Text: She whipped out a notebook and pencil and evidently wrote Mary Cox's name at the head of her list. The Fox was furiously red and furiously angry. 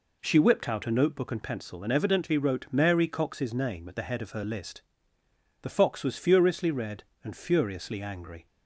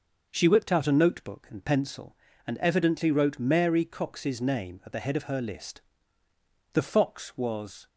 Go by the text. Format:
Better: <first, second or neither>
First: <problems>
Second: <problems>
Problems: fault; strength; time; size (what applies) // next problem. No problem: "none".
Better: first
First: none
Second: stops before "furiously red and furiously angry"; at 7.8 s